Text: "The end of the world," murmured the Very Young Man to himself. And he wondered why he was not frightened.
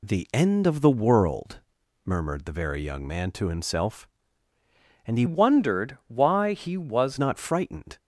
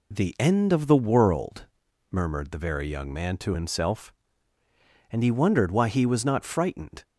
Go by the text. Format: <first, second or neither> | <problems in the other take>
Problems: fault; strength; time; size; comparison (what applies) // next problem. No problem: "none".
second | changes voice from "wondered" to "was"; from 5.2 to 7.1 s; 1.9 s long